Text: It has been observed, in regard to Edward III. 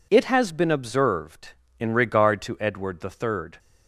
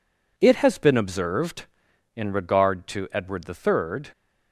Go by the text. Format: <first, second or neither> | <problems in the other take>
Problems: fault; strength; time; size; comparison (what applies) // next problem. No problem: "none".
neither | none